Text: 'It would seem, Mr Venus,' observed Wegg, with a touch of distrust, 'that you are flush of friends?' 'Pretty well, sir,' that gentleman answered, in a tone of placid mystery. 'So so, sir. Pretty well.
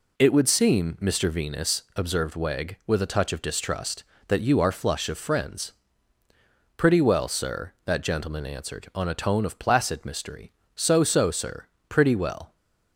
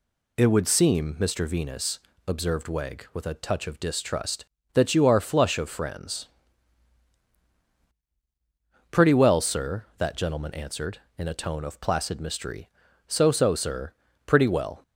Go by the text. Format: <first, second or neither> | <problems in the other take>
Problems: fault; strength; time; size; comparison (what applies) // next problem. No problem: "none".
second | says "on" for "in"; at 8.9 s